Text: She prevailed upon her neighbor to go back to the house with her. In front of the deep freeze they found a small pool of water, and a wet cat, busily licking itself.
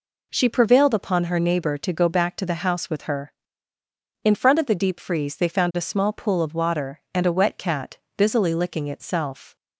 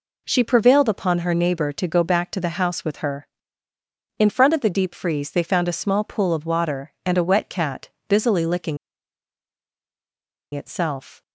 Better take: first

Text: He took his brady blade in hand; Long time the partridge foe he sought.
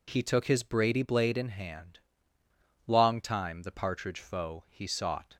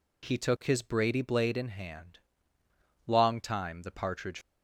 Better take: first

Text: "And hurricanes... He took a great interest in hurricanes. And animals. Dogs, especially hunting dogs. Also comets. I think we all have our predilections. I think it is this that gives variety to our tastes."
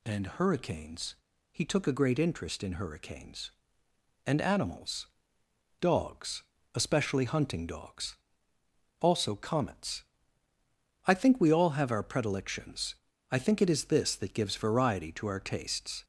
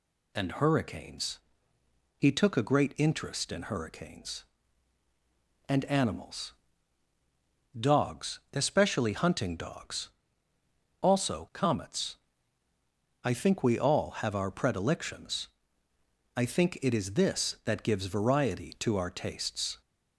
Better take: neither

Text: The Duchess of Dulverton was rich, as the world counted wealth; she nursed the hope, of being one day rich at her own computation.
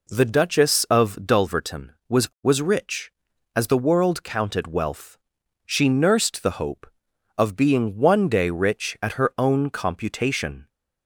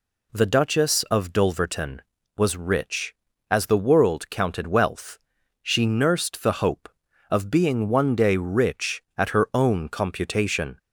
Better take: second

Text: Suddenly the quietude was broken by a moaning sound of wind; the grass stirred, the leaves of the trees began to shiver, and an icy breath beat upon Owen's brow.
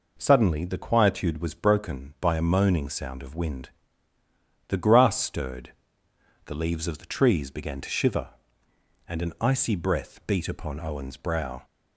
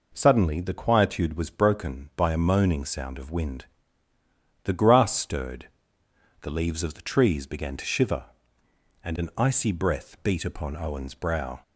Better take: neither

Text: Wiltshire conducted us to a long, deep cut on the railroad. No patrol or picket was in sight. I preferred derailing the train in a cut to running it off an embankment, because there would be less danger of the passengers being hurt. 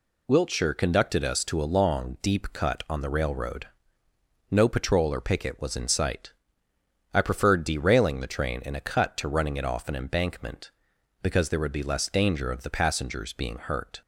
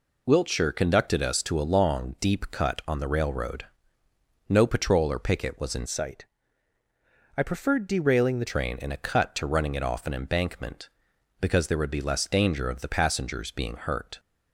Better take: first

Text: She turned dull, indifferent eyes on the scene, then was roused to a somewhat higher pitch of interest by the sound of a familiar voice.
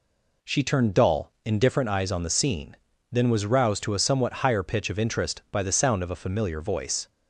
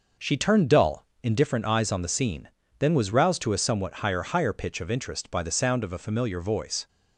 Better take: first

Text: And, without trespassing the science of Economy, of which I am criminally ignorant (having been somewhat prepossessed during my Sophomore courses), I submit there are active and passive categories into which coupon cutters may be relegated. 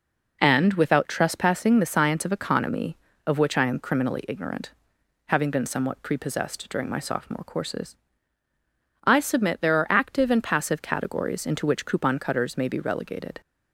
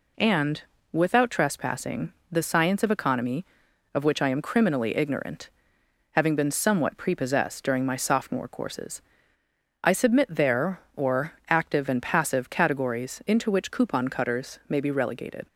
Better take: first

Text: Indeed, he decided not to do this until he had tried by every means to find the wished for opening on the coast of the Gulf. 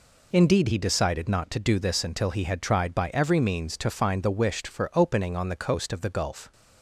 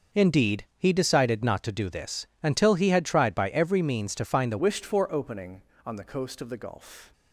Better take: first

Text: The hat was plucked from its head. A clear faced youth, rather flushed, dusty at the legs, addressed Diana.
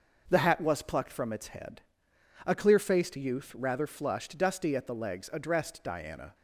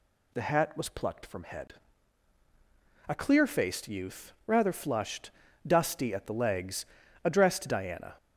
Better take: first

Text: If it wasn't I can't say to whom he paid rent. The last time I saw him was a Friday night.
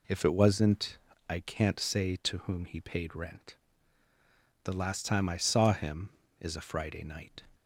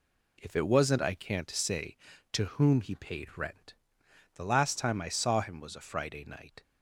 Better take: second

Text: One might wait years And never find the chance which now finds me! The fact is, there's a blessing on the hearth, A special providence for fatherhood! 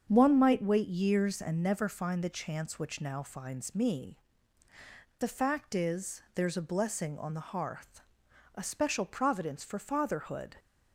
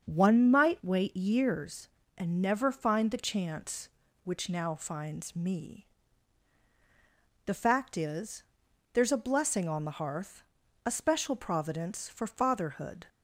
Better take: neither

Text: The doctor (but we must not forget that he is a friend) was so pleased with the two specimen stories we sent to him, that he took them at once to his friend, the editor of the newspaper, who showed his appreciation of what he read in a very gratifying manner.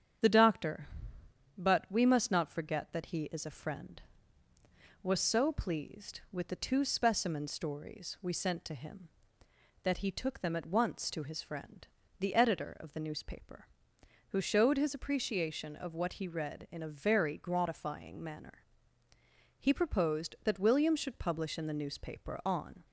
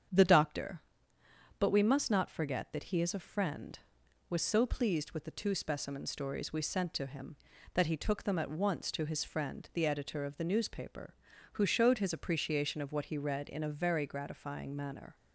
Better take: second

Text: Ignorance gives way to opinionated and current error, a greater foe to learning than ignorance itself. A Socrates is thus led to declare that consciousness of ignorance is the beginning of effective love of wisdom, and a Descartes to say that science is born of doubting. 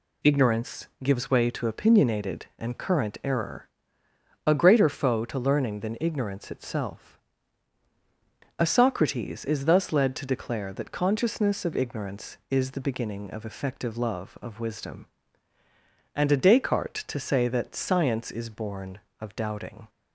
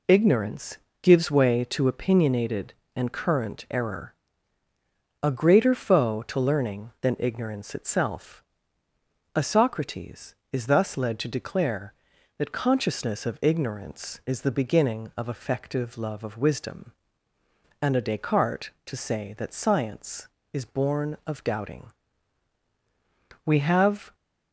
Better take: first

